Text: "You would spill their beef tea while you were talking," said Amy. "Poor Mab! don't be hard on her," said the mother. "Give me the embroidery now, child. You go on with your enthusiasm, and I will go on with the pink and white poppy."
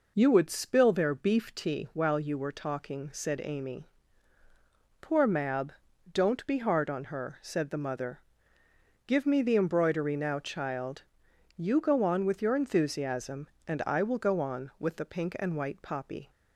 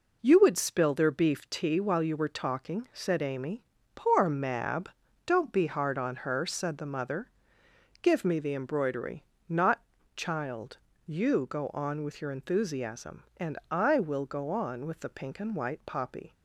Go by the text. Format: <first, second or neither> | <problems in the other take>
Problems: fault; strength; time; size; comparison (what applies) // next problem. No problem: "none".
first | says "not" for "now"; at 9.4 s